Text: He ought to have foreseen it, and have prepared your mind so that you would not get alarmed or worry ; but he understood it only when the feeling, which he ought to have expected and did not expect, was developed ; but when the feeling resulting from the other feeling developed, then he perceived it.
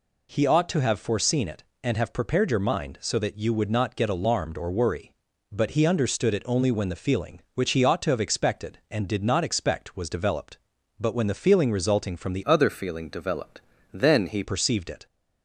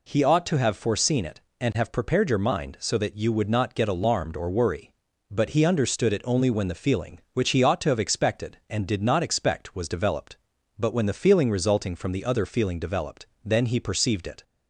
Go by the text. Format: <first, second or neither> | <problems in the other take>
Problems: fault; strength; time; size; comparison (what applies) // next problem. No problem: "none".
second | changes voice from "other" to "he"; from 12.4 to 14.4 s; 2.0 s long